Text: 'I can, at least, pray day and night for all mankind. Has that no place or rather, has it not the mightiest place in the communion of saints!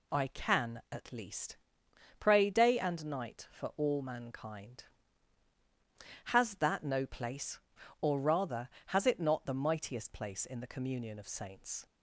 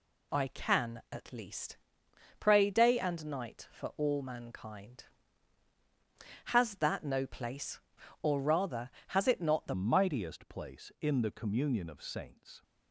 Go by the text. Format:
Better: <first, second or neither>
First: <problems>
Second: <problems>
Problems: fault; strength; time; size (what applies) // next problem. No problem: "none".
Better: first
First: none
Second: changes voice at "mightiest"; from 9.7 s on; 2.9 s long